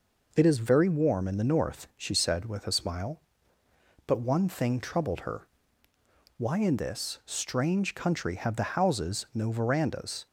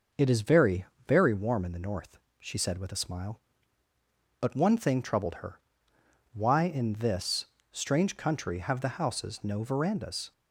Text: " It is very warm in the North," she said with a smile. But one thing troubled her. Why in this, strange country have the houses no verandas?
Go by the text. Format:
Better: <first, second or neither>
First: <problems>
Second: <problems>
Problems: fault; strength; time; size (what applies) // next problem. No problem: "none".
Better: first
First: none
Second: says "very" twice; at 1.0 s